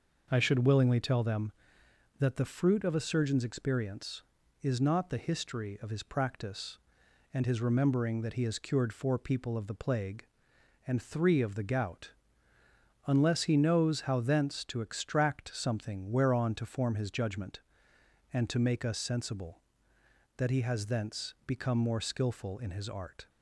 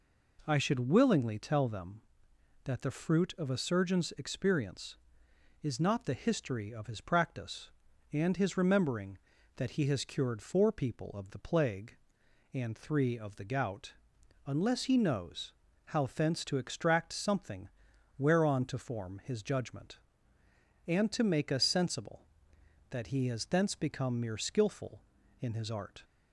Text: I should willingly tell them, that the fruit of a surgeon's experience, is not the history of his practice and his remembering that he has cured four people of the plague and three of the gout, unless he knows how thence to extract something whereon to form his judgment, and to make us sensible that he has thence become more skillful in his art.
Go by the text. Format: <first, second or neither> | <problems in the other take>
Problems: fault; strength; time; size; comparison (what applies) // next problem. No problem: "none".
first | pauses between "knows" and "how"; slight; at 15.5 s; 0.34 s long // pauses between "something" and "whereon"; noticeable; at 17.6 s; 0.50 s long // says "mere" for "more"; at 24.1 s